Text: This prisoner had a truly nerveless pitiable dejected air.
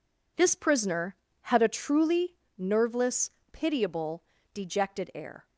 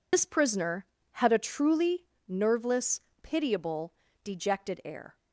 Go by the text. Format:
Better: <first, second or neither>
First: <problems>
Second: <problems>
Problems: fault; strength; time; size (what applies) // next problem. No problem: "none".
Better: first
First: pauses between "truly" and "nerveless"; slight; at 2.3 s; 0.22 s long // pauses between "nerveless" and "pitiable"; slight; at 3.2 s; 0.22 s long // pauses between "pitiable" and "dejected"; slight; at 4.2 s; 0.32 s long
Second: loses the start of "This"; at 0.1 s; 75 ms // pauses between "truly" and "nerveless"; slight; at 2.0 s; 0.22 s long // pauses between "nerveless" and "pitiable"; slight; at 2.9 s; 0.22 s long // pauses between "pitiable" and "dejected"; slight; at 3.9 s; 0.32 s long